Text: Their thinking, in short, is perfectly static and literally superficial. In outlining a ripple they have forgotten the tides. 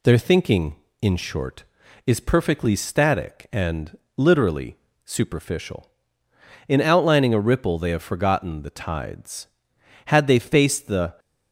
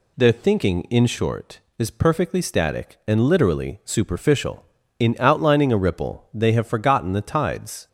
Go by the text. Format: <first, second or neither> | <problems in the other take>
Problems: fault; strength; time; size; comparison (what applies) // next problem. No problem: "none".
second | pauses between "and" and "literally"; slight; at 3.9 s; 0.20 s long // pauses between "literally" and "superficial"; slight; at 4.7 s; 0.28 s long // goes on to say "Had they faced the"; noticeable; from 10.0 s on; 1.1 s long